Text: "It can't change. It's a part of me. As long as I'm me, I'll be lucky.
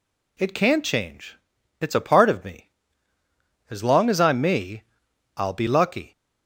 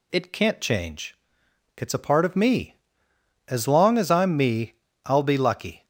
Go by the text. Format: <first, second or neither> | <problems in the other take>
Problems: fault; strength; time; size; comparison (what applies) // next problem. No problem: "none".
neither | none